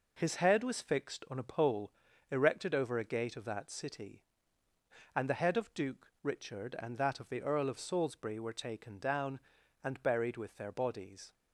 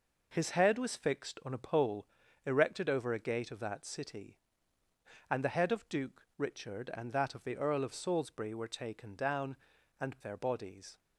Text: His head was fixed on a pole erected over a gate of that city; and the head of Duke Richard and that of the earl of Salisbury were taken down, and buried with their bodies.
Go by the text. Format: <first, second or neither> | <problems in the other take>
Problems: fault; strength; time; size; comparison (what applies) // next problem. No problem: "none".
first | pauses between "pole" and "erected"; at 2.0 s; 0.40 s long; also in the first // skips "buried with"; at 10.1 s